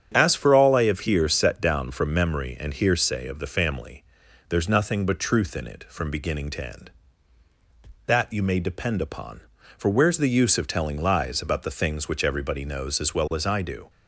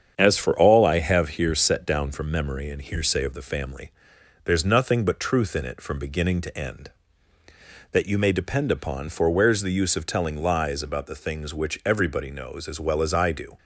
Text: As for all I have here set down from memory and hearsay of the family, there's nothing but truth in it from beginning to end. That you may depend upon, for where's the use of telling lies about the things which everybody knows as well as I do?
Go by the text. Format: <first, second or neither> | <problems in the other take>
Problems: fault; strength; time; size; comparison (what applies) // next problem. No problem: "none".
neither | starts louder than the rest; strong; the same in both